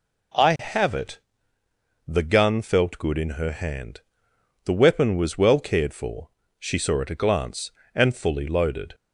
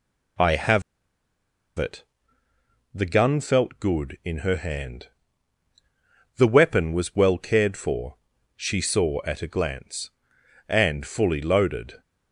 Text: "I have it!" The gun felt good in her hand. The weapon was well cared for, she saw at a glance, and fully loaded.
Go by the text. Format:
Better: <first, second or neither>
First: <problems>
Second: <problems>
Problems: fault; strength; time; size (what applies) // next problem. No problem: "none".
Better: first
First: none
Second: pauses between "have" and "it"; noticeable; at 0.8 s; 0.96 s long